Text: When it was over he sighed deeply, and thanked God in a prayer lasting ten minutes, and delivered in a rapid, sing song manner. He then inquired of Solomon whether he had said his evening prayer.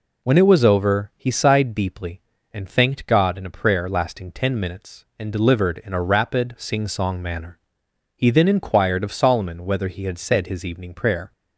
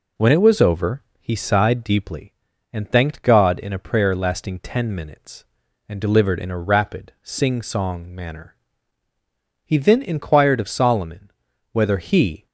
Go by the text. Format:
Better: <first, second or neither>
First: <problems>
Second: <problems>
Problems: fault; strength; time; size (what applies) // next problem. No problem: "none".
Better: first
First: none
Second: pauses between "over" and "he"; slight; at 1.0 s; 0.18 s long // pauses between "Solomon" and "whether"; at 11.2 s; 0.42 s long // stops before "had said his evening prayer"; at 12.4 s